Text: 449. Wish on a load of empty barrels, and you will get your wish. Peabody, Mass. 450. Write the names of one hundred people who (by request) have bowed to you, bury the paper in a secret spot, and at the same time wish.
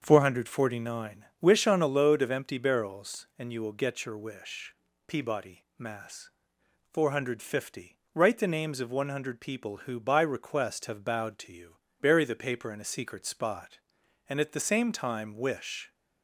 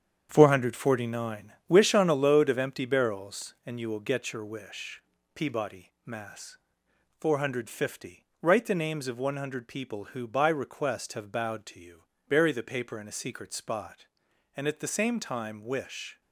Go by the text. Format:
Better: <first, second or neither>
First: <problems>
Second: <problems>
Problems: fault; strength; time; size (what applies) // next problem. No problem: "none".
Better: first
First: starts louder than the rest; until 1.0 s; 6.5 dB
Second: gets quieter; strong; throughout; 8 dB // starts louder than the rest; strong; until 1.3 s; 8 dB